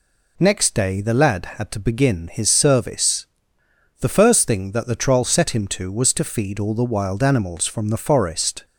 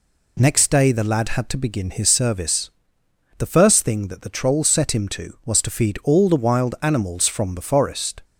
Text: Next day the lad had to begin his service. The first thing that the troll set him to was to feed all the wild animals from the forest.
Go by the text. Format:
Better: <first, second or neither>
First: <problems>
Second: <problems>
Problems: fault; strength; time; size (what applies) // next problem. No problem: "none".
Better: neither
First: none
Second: none